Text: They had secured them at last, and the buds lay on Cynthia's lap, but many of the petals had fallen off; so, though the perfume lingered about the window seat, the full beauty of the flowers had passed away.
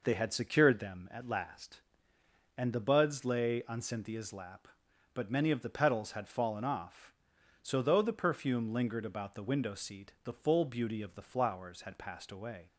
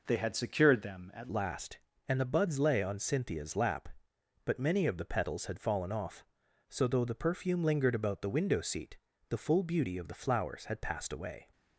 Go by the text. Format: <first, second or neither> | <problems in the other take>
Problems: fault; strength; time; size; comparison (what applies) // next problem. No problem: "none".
first | changes voice at "last"; from 1.3 s on; 10.1 s long